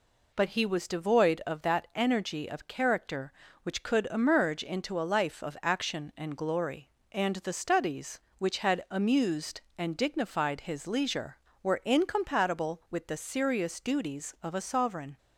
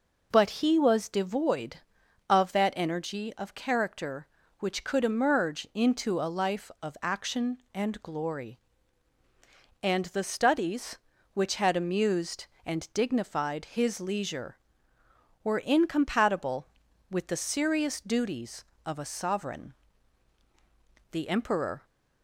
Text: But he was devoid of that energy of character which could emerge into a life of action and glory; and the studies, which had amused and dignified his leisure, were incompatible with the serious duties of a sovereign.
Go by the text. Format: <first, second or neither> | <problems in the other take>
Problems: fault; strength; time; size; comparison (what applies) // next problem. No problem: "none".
first | goes on to say "The emperor"; noticeable; from 21.1 s on; 0.72 s long